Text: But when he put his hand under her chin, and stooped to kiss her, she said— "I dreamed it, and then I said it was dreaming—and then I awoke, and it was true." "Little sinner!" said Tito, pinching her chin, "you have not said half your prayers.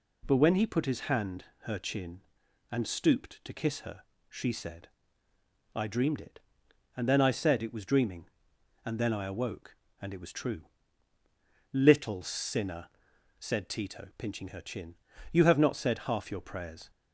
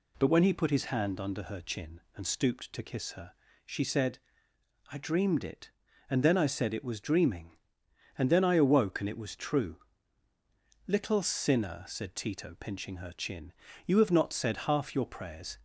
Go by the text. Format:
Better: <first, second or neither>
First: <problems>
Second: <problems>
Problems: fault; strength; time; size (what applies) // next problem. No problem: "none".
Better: second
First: skips "under"; at 1.5 s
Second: none